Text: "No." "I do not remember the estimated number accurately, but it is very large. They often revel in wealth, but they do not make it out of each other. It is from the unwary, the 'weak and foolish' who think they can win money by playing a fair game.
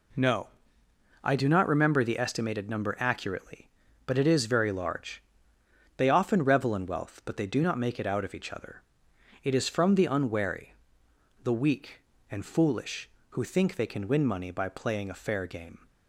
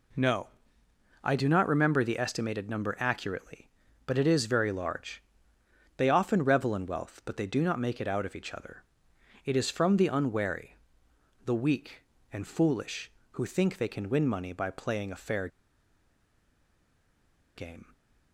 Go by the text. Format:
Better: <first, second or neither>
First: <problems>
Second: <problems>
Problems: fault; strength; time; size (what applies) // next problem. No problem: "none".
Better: first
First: none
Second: pauses between "fair" and "game"; strong; at 15.4 s; 2.0 s long